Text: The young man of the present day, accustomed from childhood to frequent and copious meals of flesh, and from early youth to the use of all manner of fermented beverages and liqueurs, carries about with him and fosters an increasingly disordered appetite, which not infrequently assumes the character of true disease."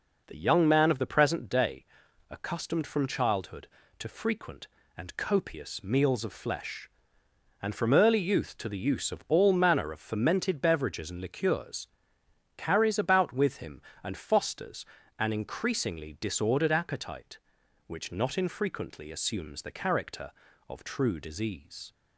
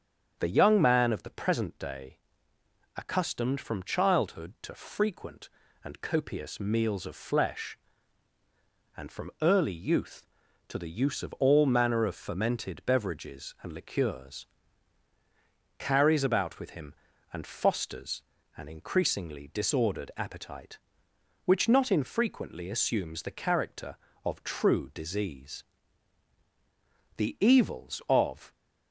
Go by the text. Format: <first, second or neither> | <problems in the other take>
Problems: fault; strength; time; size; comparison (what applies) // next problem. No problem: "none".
first | starts louder than the rest; strong; until 1.3 s; 8 dB // pauses between "fosters" and "an"; slight; at 18.2 s; 0.36 s long; slight in the first // goes on to say "The evils of"; from 27.1 s on; 1.3 s long